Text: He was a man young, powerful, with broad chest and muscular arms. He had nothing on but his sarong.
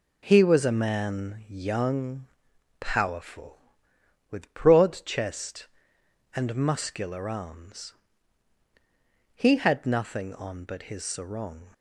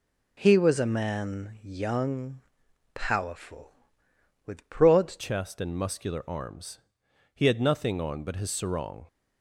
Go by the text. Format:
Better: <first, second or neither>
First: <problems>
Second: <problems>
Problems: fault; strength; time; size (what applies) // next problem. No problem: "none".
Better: first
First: none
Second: changes voice at "chest"; from 5.1 s on; 3.9 s long